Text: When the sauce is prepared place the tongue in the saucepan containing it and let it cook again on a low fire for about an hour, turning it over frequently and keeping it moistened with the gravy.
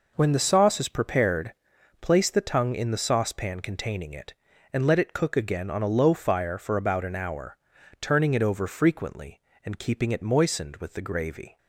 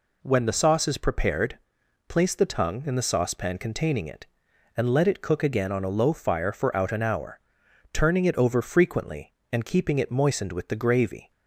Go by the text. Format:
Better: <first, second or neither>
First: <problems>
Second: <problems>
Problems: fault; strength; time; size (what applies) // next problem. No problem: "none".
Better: first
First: pauses between "prepared" and "place"; noticeable; at 1.5 s; 0.46 s long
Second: pauses between "prepared" and "place"; noticeable; at 1.5 s; 0.50 s long // says "out" for "about"; at 6.7 s